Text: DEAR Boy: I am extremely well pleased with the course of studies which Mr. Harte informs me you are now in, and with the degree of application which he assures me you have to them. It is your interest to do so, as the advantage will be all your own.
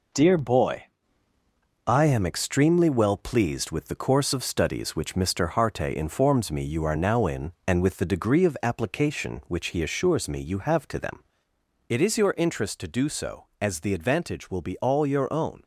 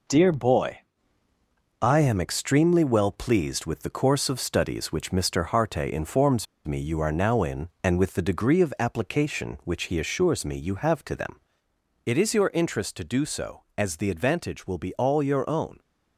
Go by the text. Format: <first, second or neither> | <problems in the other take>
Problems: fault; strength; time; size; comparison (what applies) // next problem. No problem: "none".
first | pauses between "informs" and "me"; slight; at 6.4 s; 0.22 s long